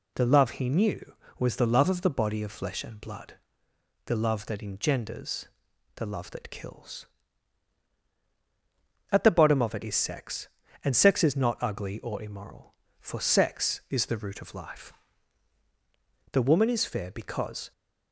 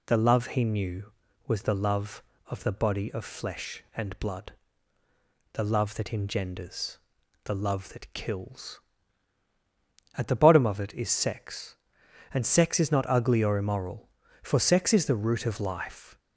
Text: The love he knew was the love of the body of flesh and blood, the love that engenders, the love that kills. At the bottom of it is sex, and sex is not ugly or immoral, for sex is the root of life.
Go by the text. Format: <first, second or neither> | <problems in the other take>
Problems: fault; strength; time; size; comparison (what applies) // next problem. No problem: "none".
second | goes on to say "The woman is fair because"; from 16.3 s on; 1.3 s long